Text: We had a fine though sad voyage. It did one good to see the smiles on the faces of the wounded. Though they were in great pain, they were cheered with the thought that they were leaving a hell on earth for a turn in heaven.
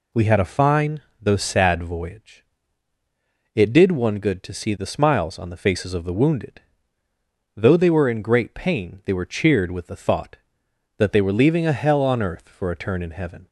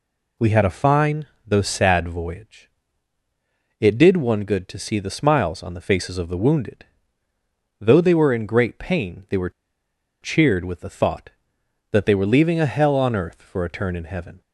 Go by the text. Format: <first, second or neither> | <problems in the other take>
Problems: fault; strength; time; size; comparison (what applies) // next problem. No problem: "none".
first | pauses between "fine" and "though"; slight; at 1.2 s; 0.22 s long; slight in the first // pauses between "were" and "cheered"; noticeable; at 9.4 s; 0.72 s long